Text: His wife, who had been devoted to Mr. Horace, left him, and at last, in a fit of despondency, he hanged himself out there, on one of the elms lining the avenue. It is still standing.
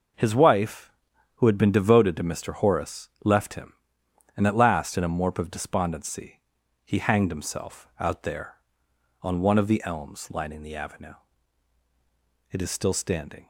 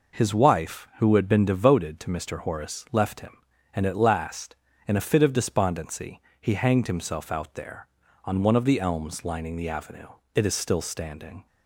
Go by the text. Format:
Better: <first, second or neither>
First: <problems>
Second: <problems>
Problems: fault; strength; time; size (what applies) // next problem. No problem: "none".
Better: second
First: says "morp" for "fit"; at 5.0 s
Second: none